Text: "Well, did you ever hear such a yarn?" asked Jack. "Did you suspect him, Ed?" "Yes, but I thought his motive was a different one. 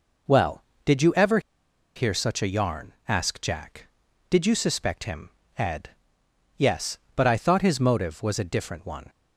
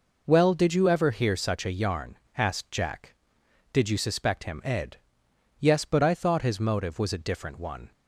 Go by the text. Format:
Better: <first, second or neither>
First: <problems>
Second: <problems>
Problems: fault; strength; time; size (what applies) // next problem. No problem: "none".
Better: second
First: pauses between "ever" and "hear"; noticeable; at 1.3 s; 0.55 s long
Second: none